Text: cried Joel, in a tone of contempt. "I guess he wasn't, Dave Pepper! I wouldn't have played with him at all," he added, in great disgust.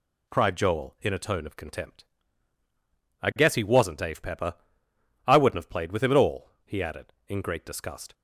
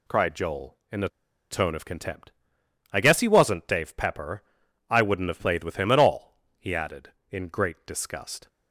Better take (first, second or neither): first